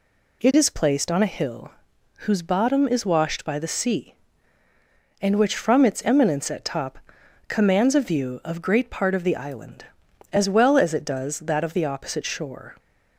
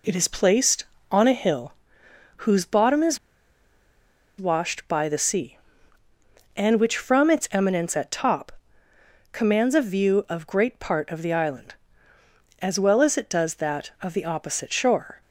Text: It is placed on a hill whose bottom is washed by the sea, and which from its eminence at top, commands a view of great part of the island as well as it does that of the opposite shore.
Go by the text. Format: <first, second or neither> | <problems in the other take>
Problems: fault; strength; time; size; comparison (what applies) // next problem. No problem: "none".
first | pauses between "hill" and "whose"; noticeable; at 1.7 s; 0.64 s long; noticeable in the first // pauses between "is" and "washed"; at 3.1 s; 1.2 s long